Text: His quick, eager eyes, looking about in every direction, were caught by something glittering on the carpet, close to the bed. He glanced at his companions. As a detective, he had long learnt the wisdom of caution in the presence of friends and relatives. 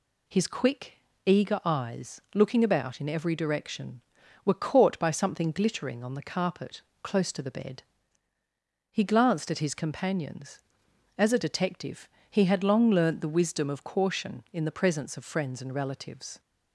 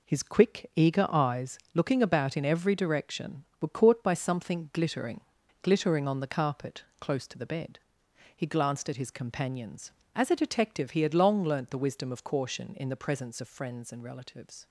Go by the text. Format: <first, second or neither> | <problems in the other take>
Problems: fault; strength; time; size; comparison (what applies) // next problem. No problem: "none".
first | says "glittering" twice; at 5.6 s